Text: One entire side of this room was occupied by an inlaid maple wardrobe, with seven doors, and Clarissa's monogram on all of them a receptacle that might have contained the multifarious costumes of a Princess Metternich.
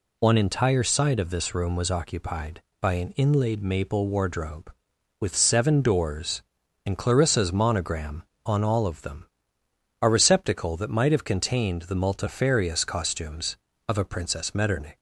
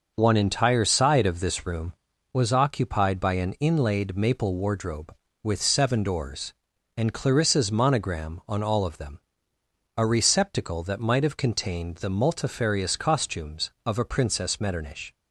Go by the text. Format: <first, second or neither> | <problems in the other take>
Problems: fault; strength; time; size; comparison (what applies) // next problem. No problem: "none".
neither | pauses between "them" and "a"; noticeable; the same in both